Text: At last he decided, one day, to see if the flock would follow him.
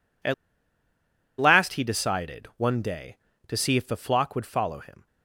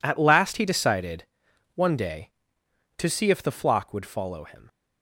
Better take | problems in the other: second | pauses between "At" and "last"; at 0.3 s; 1.0 s long

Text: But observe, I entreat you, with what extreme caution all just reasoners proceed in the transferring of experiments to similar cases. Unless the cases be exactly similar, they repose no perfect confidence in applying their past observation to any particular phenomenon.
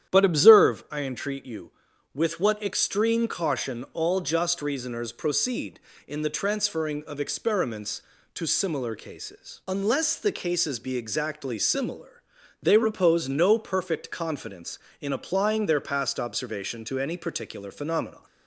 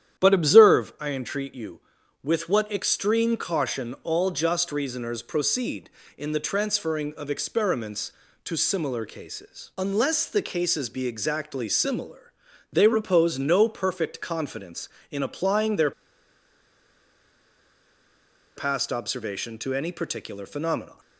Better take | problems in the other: first | starts louder than the rest; strong; until 1.2 s; 10 dB; strong in the first // pauses between "their" and "past"; strong; at 15.9 s; 2.6 s long

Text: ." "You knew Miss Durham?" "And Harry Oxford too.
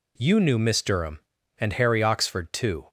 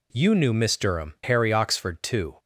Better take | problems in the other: first | skips "And"; at 1.1 s

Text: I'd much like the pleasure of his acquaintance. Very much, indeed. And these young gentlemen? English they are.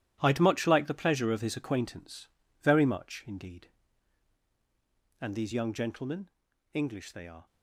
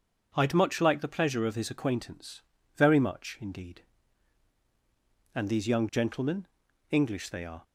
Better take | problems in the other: second | gets quieter; strong; throughout; 11 dB

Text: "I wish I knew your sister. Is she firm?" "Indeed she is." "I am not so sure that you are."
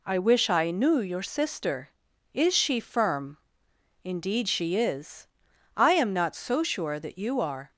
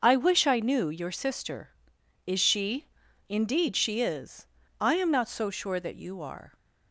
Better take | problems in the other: first | starts louder than the rest; until 1.0 s; 6 dB // skips "firm"; at 3.0 s

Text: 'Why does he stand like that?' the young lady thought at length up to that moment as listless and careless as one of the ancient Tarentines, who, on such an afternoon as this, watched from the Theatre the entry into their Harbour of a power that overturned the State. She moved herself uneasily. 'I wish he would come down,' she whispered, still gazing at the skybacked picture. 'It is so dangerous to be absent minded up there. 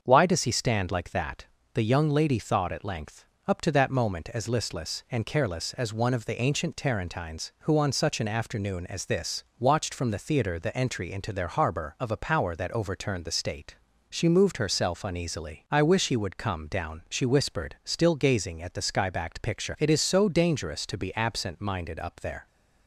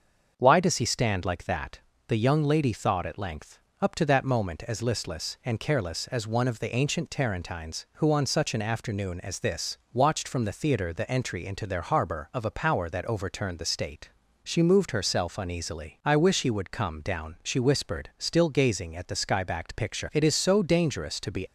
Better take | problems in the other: first | starts louder than the rest; until 1.3 s; 7 dB; also in the first // pauses between "length" and "up"; slight; at 3.5 s; 0.22 s long; slight in the first // stops before "absent minded up there"; at 21.4 s

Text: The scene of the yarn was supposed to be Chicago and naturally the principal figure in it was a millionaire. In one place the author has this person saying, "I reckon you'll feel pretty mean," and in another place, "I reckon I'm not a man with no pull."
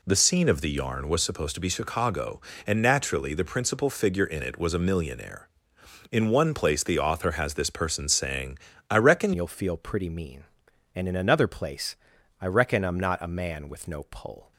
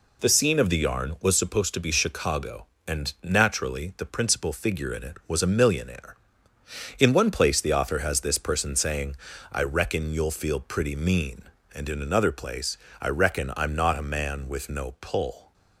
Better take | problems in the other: second | changes voice at "you'll"; from 9.3 s on; 5.2 s long

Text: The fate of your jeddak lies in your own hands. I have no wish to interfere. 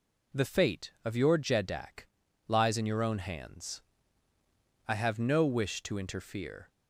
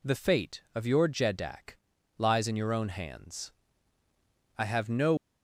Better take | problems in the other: first | pauses between "jeddak" and "lies"; at 1.7 s; 0.40 s long; also in the first // stops before "wish to interfere"; at 5.1 s

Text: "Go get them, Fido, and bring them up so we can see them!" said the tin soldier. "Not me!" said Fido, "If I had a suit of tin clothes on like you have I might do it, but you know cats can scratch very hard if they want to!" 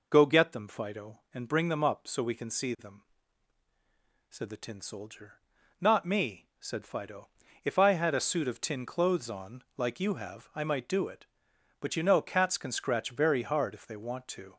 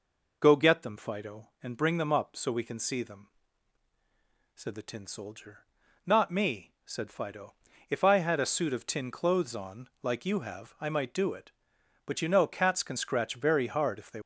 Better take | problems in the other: first | stops before "want to"; at 14.2 s

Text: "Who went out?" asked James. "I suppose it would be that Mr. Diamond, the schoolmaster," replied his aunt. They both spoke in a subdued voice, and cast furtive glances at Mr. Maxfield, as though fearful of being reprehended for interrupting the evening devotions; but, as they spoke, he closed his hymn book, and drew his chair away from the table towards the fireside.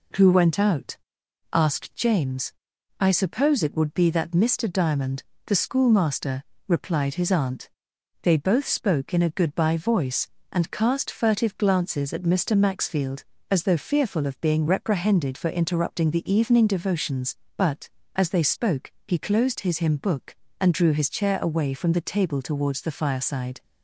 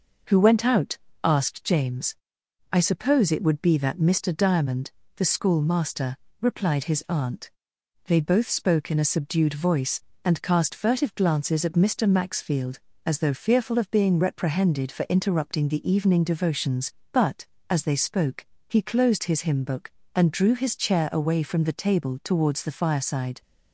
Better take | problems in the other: second | says "goodbye" for "subdued"; at 9.3 s

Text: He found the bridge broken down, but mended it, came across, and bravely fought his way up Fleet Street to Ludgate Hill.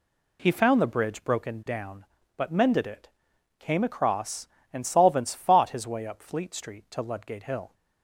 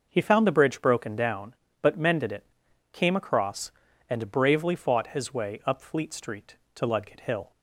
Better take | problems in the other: second | says "solvents" for "bravely"; at 4.8 s

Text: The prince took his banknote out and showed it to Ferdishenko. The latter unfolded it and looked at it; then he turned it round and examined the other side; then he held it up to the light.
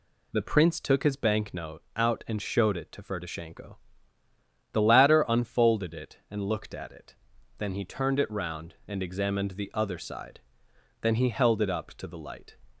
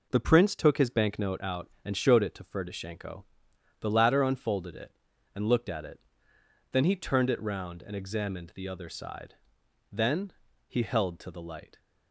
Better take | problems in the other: first | pauses between "then" and "he"; slight; at 10.3 s; 0.36 s long // skips "it up"; at 11.1 s

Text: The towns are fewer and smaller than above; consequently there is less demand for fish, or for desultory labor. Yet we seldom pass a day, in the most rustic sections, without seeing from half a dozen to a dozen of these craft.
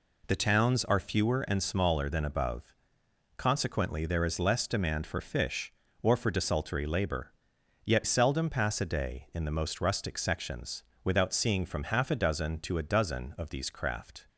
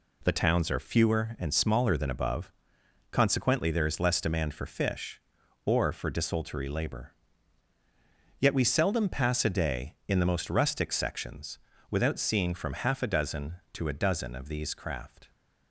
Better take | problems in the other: second | skips "we"; at 8.0 s

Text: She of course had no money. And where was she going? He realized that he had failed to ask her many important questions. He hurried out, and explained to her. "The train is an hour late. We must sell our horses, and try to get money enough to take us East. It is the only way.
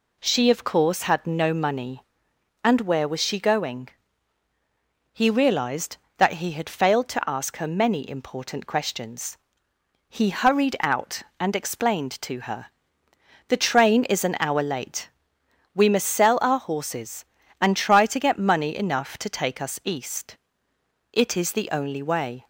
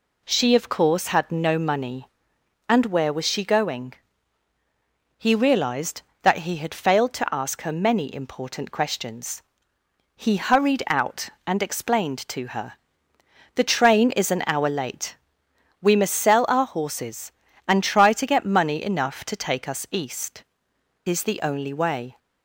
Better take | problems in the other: first | skips "It"; at 20.7 s

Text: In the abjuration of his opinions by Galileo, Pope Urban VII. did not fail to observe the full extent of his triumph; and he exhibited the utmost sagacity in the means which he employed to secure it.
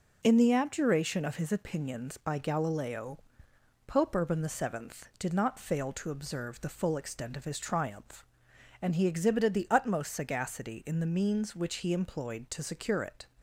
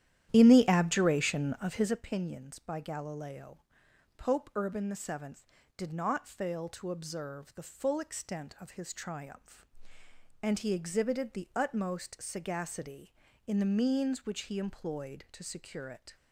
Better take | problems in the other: first | starts louder than the rest; strong; until 2.1 s; 11.5 dB

